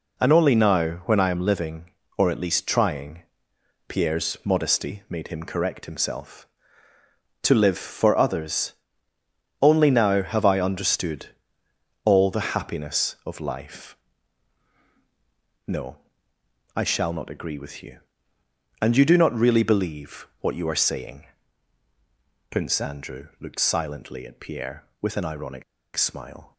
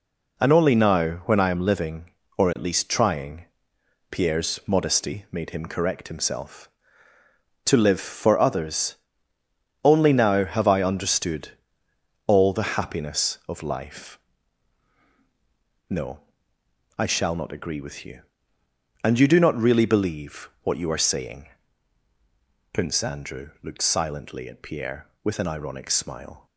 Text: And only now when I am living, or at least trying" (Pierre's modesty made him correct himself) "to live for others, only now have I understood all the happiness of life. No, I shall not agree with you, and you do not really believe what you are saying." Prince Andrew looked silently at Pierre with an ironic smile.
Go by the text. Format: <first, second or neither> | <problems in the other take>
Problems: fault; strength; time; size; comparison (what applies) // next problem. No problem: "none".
second | pauses between "understood" and "all"; noticeable; at 11.2 s; 0.76 s long; noticeable in the second // pauses between "ironic" and "smile"; slight; at 25.6 s; 0.32 s long